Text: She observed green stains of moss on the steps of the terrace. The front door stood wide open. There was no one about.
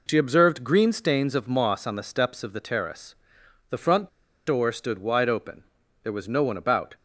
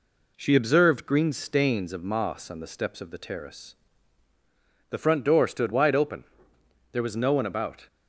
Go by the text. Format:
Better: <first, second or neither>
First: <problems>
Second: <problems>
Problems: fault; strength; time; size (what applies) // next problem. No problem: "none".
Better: second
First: pauses between "front" and "door"; at 4.0 s; 0.39 s long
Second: none